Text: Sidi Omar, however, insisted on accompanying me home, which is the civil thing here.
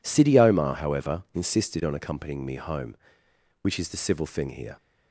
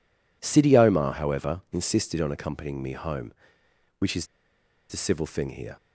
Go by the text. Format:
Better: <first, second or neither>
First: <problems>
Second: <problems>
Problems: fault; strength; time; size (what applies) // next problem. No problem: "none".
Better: first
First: none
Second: pauses between "is" and "the"; noticeable; at 4.2 s; 0.63 s long